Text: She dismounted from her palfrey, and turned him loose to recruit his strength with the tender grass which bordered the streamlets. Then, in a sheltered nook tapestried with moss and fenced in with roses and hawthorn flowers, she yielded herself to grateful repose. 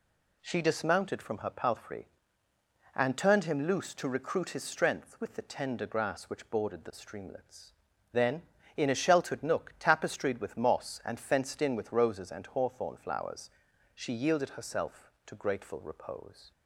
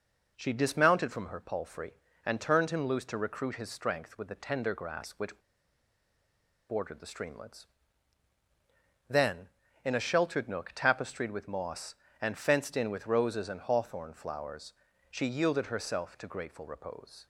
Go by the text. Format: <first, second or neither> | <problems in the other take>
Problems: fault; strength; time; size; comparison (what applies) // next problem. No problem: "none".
first | pauses between "which" and "bordered"; strong; at 5.3 s; 1.3 s long